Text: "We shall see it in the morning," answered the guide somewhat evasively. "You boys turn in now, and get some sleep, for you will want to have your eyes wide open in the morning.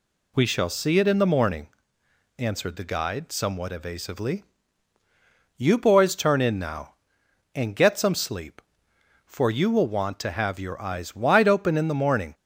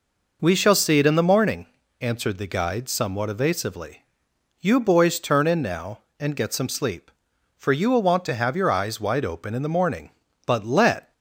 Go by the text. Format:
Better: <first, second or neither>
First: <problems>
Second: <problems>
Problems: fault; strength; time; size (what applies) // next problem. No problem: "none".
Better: first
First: none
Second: goes on to say "But let"; noticeable; from 10.4 s on; 0.66 s long